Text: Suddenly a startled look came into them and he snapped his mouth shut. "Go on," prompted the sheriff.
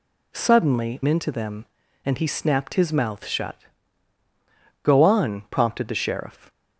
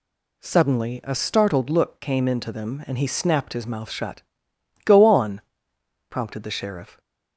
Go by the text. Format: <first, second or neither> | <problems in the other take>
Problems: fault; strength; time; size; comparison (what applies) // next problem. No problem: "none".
second | skips "a startled look came"; at 1.0 s